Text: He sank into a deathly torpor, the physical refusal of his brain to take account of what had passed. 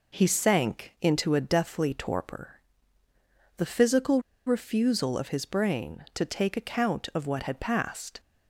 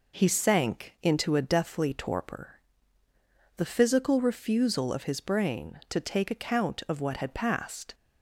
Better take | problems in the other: second | pauses between "physical" and "refusal"; slight; at 4.2 s; 0.25 s long

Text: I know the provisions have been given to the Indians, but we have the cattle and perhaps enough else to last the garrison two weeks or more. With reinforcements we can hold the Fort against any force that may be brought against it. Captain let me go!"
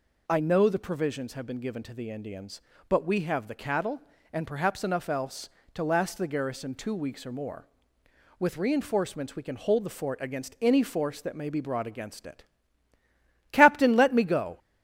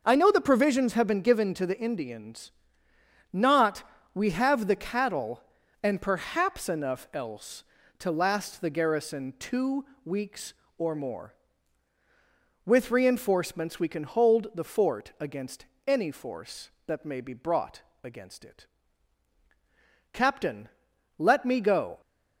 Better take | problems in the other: first | starts louder than the rest; noticeable; until 1.0 s; 6 dB // says "not" for "but"; at 3.3 s // pauses between "two" and "weeks"; slight; at 9.8 s; 0.20 s long // pauses between "against" and "any"; slight; at 15.6 s; 0.20 s long // pauses between "brought" and "against"; slight; at 17.8 s; 0.20 s long // pauses between "Captain" and "let"; noticeable; at 20.6 s; 0.50 s long

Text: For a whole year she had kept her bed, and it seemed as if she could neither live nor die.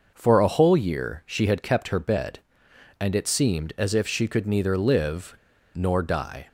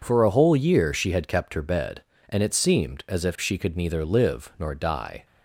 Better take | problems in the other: second | pauses between "live" and "nor"; at 5.3 s; 0.41 s long

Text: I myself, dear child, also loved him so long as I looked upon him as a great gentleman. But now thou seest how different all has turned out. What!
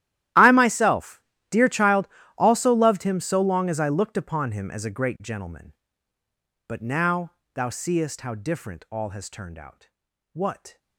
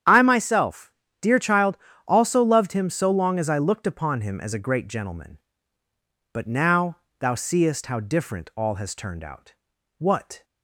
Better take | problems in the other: second | gets quieter; strong; throughout; 21.5 dB // starts louder than the rest; strong; until 1.6 s; 13 dB; strong in the second // pauses between "now" and "thou"; slight; at 7.3 s; 0.20 s long; slight in the second

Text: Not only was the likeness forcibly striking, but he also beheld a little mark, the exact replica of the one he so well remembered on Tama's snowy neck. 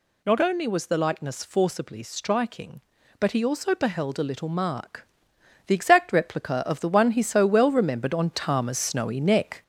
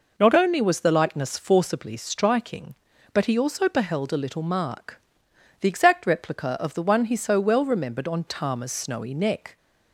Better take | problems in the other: second | gets louder; noticeable; throughout; 4 dB

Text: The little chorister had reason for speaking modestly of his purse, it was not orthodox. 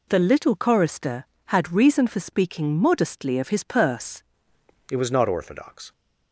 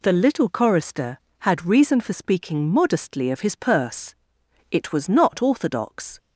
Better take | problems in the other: second | changes voice at "it"; from 4.9 s on; 1.0 s long

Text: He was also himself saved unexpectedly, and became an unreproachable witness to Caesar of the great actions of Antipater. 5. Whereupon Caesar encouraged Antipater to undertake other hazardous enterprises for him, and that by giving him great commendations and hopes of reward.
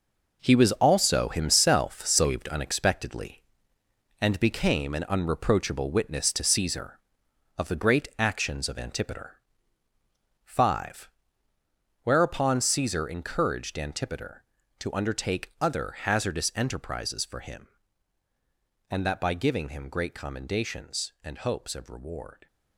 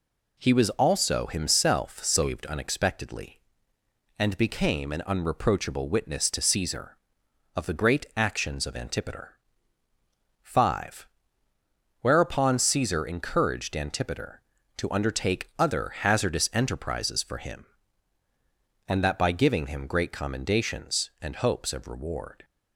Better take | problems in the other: second | gets quieter; strong; throughout; 9.5 dB

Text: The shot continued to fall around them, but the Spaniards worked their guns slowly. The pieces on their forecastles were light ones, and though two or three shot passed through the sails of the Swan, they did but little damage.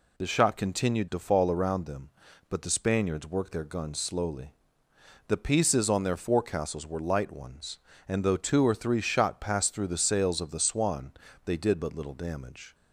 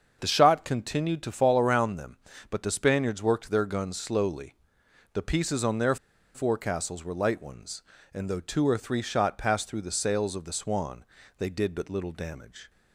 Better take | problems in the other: first | starts louder than the rest; until 1.2 s; 6.5 dB // pauses between "their" and "forecastles"; at 5.9 s; 0.38 s long

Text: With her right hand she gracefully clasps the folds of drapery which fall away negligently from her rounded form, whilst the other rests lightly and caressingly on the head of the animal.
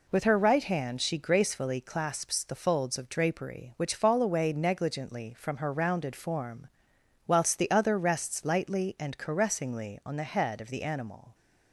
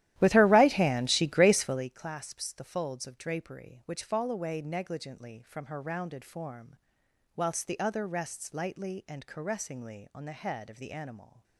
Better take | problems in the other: first | starts louder than the rest; strong; until 1.9 s; 13.5 dB

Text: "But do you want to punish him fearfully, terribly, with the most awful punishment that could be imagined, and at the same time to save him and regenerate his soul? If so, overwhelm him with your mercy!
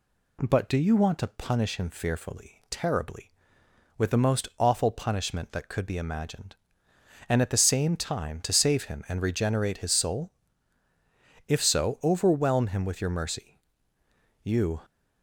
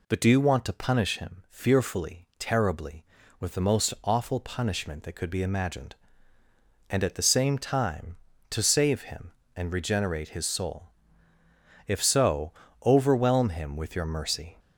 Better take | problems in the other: second | goes on to say "You"; slight; from 14.4 s on; 0.40 s long

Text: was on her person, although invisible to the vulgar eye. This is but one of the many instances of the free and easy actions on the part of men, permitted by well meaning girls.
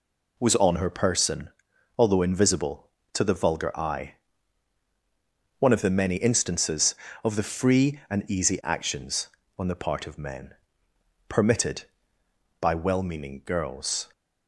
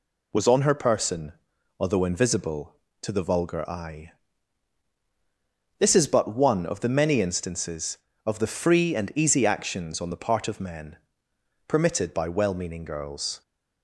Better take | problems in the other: second | skips "This is but"; at 4.8 s

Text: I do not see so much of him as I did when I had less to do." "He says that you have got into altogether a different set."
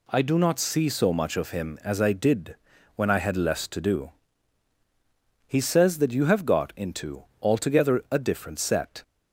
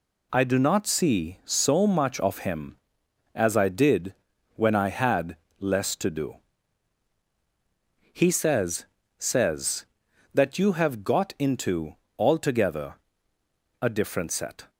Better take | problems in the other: first | pauses between "did" and "when"; at 4.1 s; 0.40 s long; also in the first // pauses between "had" and "less"; slight; at 5.3 s; 0.22 s long // says "says" twice; at 9.1 s // pauses between "into" and "altogether"; slight; at 11.9 s; 0.20 s long; slight in the first // pauses between "altogether" and "a"; noticeable; at 12.9 s; 0.88 s long

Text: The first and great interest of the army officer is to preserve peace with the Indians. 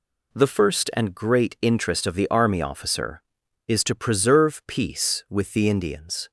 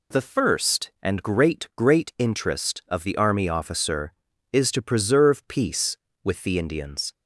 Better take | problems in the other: first | says "great" twice; at 1.7 s

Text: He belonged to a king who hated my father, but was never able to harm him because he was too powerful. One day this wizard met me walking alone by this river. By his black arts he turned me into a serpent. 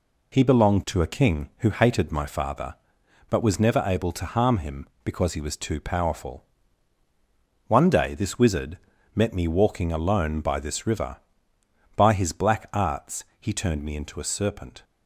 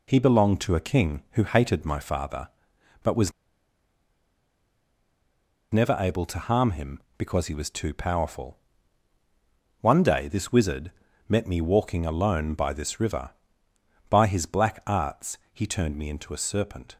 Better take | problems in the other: first | pauses between "was" and "never"; strong; at 3.3 s; 2.4 s long // pauses between "wizard" and "met"; slight; at 10.9 s; 0.36 s long; slight in the first // pauses between "arts" and "he"; slight; at 15.3 s; 0.16 s long; slight in the first

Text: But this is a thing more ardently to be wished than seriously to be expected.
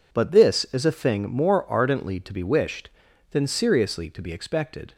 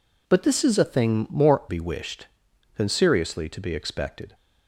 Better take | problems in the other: first | skips "ardently to"; at 1.6 s

